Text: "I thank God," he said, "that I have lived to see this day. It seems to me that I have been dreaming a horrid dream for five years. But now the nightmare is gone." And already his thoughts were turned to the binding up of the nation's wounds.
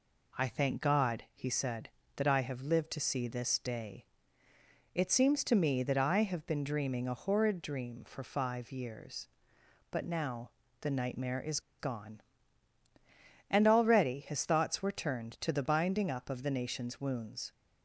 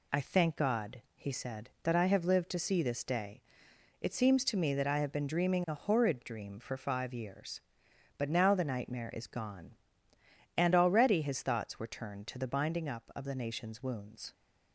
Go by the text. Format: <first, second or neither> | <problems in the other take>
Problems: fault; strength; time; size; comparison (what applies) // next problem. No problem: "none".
second | pauses between "now" and "the"; slight; at 10.5 s; 0.30 s long // pauses between "is" and "gone"; slight; at 11.5 s; 0.20 s long